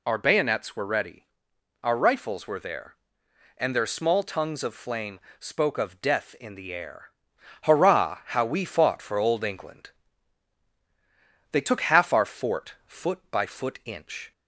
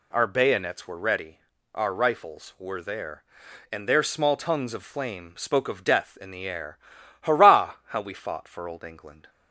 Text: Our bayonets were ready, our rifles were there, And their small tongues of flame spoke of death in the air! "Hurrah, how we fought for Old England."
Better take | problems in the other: second | pauses between "flame" and "spoke"; slight; at 5.1 s; 0.18 s long // goes on to say "They took half our fort foot by foot inch"; strong; from 11.5 s on; 2.8 s long

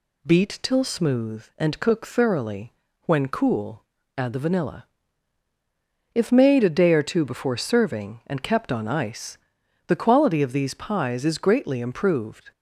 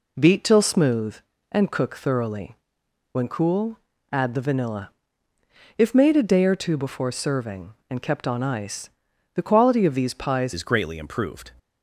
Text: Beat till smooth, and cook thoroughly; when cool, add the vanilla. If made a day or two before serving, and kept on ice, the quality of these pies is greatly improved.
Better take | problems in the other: first | changes voice at "is"; from 10.5 s on; 0.9 s long

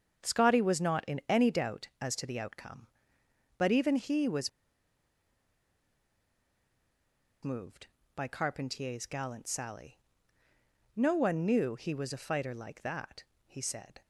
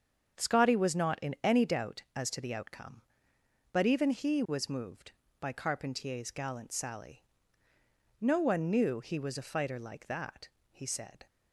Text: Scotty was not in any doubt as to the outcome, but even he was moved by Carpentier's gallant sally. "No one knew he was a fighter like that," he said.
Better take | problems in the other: second | starts louder than the rest; strong; until 1.3 s; 7.5 dB; strong in the second // pauses between "was" and "moved"; strong; at 4.4 s; 2.9 s long

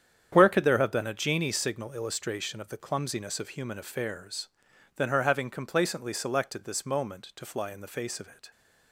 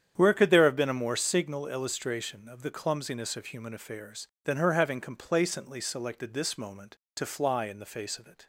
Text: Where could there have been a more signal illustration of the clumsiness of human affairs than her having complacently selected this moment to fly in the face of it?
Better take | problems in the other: second | starts louder than the rest; strong; until 1.3 s; 8.5 dB; strong in the second // says "genie" for "more"; at 1.1 s

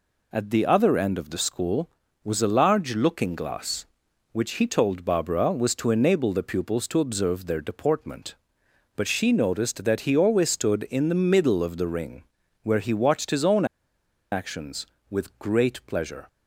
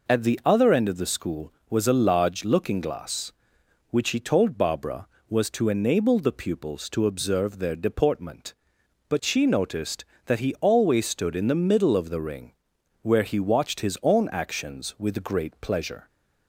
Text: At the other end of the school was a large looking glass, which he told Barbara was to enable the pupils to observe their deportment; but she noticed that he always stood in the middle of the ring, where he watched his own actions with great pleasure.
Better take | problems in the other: second | pauses between "own" and "actions"; noticeable; at 13.6 s; 0.67 s long

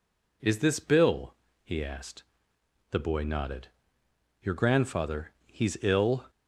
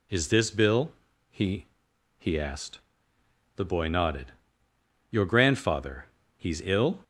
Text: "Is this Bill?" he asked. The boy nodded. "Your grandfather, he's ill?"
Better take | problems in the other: first | says "he" twice; at 2.1 s

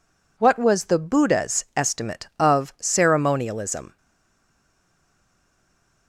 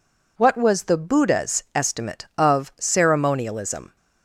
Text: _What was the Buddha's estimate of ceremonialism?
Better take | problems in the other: second | stays silent after the last word; from 3.9 s on; 2.1 s long

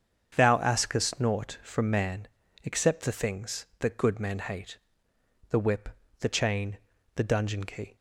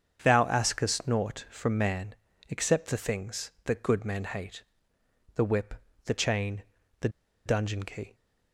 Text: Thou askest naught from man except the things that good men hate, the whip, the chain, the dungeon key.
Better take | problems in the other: first | starts louder than the rest; strong; until 1.2 s; 7.5 dB; strong in the first // pauses between "man" and "except"; slight; at 2.1 s; 0.36 s long; also in the first // pauses between "the" and "dungeon"; at 7.0 s; 0.37 s long

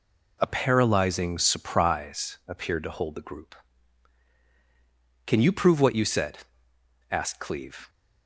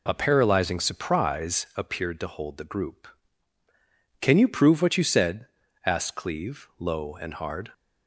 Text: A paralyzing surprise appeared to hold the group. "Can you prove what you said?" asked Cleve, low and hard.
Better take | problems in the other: second | stops before "low and hard"; at 7.8 s

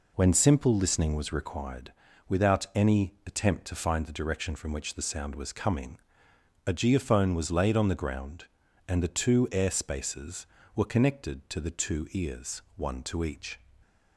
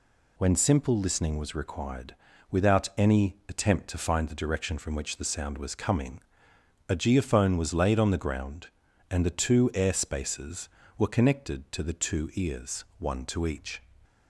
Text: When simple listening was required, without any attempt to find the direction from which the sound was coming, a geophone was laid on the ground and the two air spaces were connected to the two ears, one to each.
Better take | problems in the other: second | starts louder than the rest; until 1.6 s; 3.5 dB

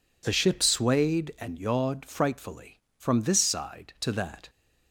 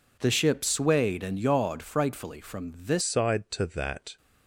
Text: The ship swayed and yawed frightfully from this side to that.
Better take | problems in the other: first | changes voice at "side"; from 3.0 s on; 1.1 s long

